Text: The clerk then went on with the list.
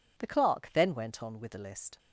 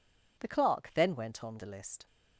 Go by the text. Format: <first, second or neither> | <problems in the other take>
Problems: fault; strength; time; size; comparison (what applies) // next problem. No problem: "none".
first | skips "with"; at 1.5 s